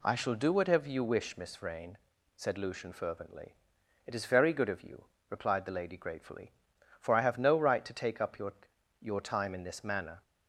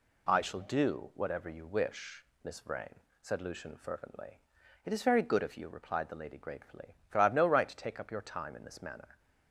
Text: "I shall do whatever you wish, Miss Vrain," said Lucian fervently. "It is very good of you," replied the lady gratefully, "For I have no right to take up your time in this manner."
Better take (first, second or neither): second